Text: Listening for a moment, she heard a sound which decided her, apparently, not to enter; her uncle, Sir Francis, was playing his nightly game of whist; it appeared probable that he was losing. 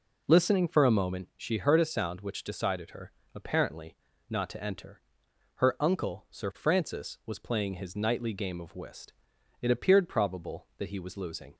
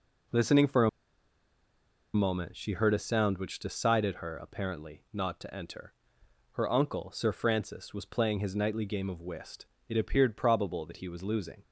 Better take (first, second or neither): first